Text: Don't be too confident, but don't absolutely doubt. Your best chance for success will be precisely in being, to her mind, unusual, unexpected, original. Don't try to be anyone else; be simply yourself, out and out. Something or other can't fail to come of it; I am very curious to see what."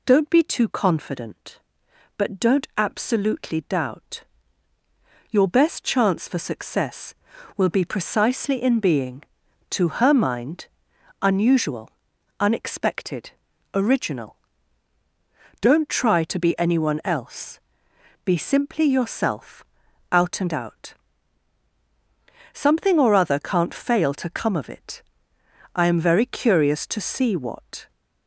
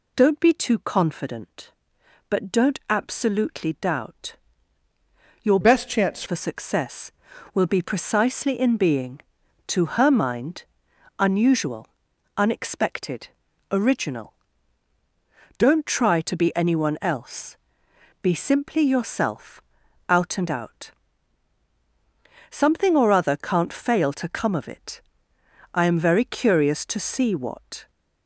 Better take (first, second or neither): first